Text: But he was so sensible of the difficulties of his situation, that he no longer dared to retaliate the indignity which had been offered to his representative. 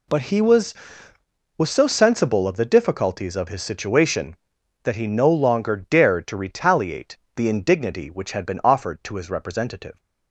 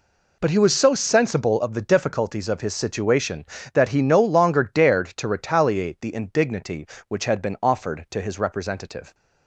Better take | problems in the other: second | says "was" twice; at 1.5 s // pauses between "retaliate" and "the"; slight; at 7.1 s; 0.20 s long

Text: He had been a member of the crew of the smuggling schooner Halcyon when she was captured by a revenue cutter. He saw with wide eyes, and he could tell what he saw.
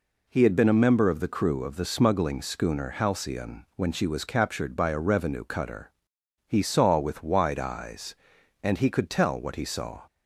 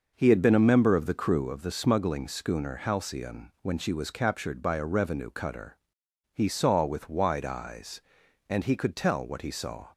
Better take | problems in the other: first | starts louder than the rest; noticeable; until 1.6 s; 6 dB

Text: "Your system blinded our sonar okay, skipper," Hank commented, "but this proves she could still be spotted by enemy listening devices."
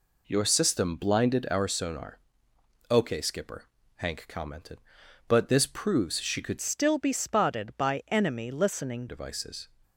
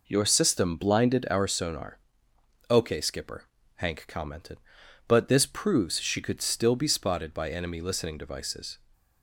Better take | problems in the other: second | pauses between "sonar" and "okay"; noticeable; at 2.1 s; 0.72 s long; noticeable in the second // changes voice from "still" to "listening"; from 6.6 to 9.0 s; 2.4 s long

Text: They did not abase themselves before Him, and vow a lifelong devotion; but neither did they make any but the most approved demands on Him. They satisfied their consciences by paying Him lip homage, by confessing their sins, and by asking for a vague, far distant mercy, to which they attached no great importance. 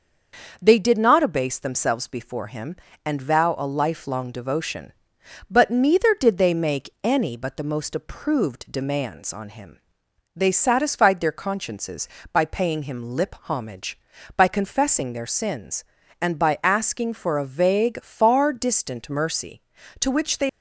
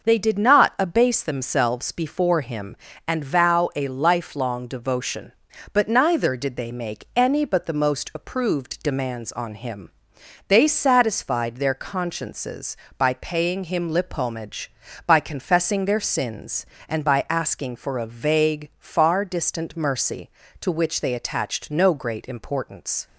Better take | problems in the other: second | starts louder than the rest; until 1.6 s; 6 dB // stops before "attached no great importance"; at 20.4 s

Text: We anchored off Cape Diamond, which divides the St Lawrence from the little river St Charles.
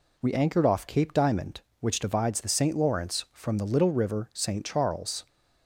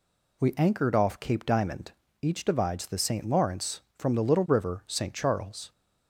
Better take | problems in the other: first | says "each" for "which"; at 2.2 s

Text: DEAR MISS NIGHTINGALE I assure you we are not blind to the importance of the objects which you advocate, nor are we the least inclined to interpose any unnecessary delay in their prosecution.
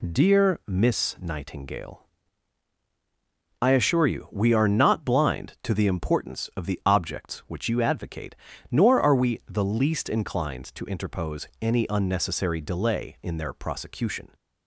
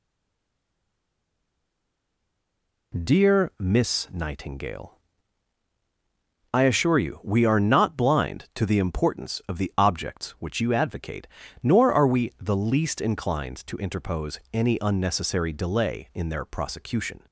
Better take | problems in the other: first | stays silent before the first word; strong; until 2.9 s; 2.9 s long // pauses between "NIGHTINGALE" and "I"; strong; at 4.9 s; 1.6 s long; strong in the first

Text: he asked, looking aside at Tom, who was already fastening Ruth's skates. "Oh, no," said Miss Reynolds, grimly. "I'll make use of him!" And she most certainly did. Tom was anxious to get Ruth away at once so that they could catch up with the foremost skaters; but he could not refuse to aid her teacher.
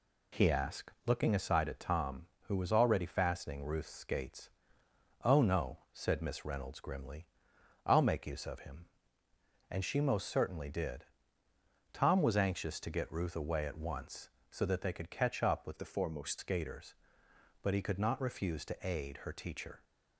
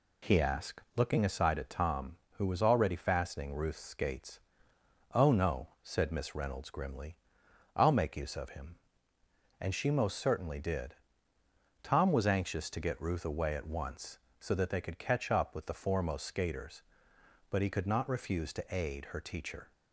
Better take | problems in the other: second | changes voice from "the" to "foremost"; from 15.7 to 16.3 s; 0.6 s long

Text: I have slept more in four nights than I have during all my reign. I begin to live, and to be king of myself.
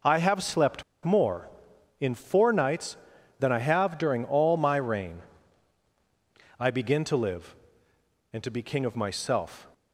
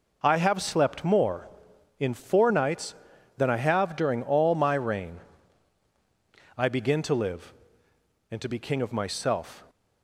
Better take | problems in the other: second | pauses between "slept" and "more"; slight; at 0.8 s; 0.21 s long

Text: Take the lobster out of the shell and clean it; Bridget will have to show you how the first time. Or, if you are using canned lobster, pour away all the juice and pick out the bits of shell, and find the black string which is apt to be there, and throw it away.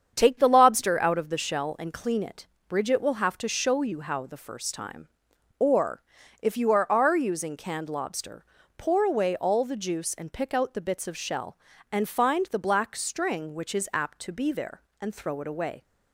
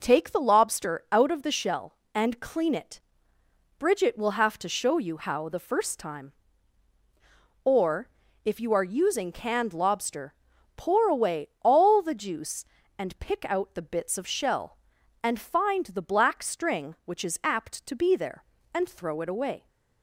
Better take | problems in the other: second | starts louder than the rest; strong; until 1.1 s; 7.5 dB // says "are" twice; at 6.9 s

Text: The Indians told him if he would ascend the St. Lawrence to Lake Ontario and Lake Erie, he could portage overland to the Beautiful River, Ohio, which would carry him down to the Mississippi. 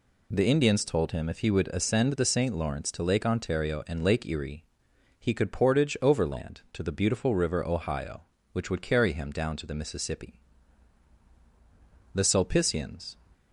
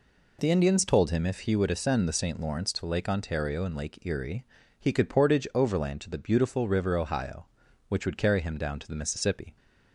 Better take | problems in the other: second | goes on to say "The Sulpicians"; noticeable; from 12.1 s on; 1.0 s long

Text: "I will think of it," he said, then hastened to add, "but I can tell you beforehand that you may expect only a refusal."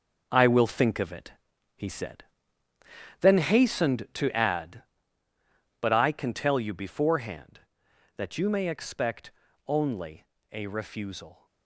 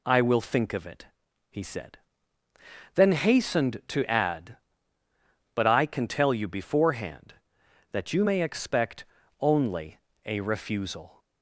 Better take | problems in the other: second | gets quieter; strong; throughout; 9 dB // pauses between "expect" and "only"; slight; at 9.3 s; 0.36 s long; slight in the second // pauses between "only" and "a"; slight; at 10.2 s; 0.26 s long; slight in the second

